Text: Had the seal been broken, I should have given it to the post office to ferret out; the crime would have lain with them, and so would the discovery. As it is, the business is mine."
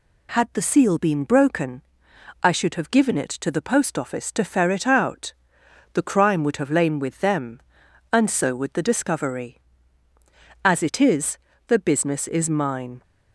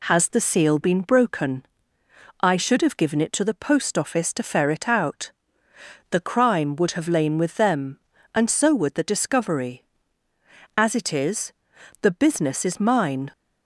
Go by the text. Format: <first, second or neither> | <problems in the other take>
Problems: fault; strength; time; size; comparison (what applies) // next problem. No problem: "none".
first | says "Has" for "Had"; at 0.0 s